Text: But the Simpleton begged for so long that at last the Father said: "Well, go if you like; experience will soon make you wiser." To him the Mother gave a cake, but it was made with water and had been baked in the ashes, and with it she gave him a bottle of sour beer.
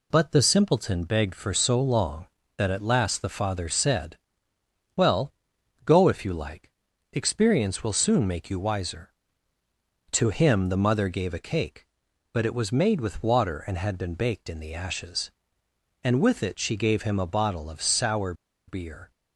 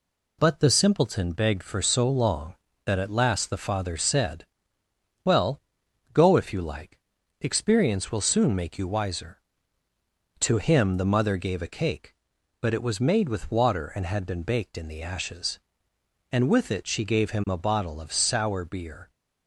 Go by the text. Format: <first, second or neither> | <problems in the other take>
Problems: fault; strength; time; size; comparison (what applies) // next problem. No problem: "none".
second | pauses between "sour" and "beer"; slight; at 18.3 s; 0.34 s long